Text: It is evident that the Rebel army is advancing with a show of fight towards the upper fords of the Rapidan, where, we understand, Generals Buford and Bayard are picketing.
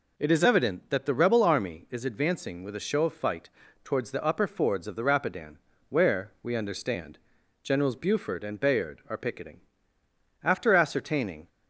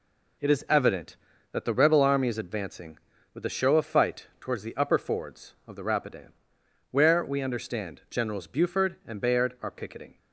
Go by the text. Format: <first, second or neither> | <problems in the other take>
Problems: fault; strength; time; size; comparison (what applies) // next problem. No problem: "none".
second | pauses between "fight" and "towards"; slight; at 3.5 s; 0.34 s long // goes on to say "After ascertaining"; noticeable; from 10.4 s on; 1.0 s long